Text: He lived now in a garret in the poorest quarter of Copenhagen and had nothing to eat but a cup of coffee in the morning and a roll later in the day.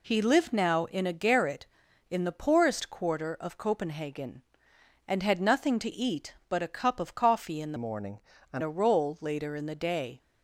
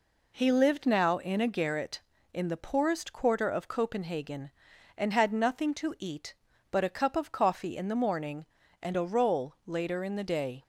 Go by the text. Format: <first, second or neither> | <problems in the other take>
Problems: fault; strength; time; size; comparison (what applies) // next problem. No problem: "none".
second | changes voice from "morning" to "and"; from 7.7 to 8.6 s; 0.9 s long